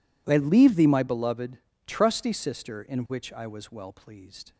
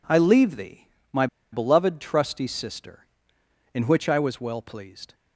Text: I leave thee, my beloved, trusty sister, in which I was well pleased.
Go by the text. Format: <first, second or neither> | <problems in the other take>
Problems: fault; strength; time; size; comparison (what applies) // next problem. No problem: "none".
first | pauses between "my" and "beloved"; slight; at 1.2 s; 0.26 s long